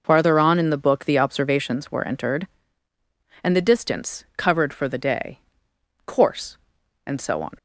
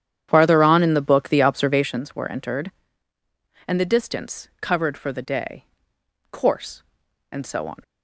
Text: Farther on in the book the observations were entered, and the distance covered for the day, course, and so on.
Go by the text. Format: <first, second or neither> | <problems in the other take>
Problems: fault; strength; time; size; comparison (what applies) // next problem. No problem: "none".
first | starts louder than the rest; strong; until 2.0 s; 9.5 dB